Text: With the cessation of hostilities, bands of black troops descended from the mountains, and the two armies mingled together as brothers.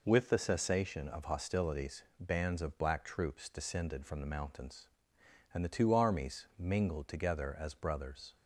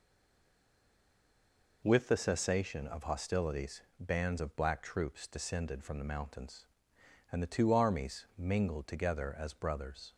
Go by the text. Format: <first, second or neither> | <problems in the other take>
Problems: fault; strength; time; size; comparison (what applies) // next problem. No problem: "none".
first | stays silent before the first word; noticeable; until 1.8 s; 1.8 s long